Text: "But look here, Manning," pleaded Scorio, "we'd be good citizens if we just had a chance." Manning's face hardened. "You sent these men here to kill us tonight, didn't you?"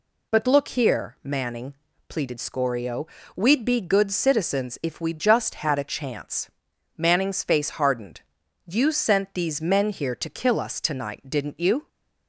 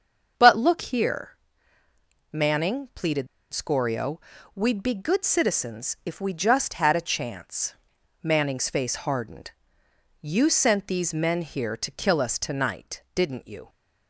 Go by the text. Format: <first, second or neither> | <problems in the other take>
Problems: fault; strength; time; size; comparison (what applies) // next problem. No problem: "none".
first | starts louder than the rest; until 1.3 s; 6.5 dB // pauses between "pleaded" and "Scorio"; slight; at 3.2 s; 0.26 s long